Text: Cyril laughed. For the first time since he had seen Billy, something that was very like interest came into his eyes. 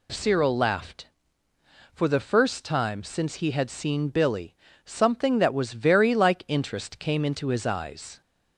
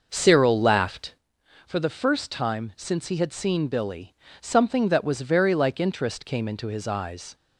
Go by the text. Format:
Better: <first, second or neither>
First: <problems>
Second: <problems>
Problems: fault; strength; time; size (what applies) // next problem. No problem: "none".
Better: first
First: none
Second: starts louder than the rest; noticeable; until 1.2 s; 6 dB